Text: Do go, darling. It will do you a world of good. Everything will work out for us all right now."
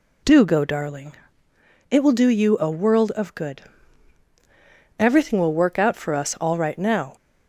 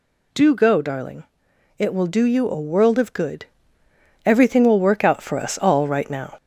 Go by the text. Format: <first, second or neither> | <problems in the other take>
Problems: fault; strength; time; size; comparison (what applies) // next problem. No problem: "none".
first | gets louder; slight; throughout; 2 dB